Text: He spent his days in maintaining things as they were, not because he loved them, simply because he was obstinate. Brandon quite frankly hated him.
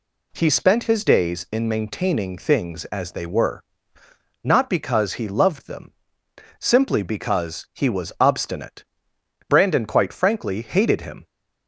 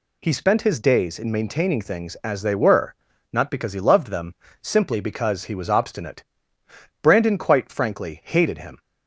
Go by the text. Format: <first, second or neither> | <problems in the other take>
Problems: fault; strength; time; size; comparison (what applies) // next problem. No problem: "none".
neither | none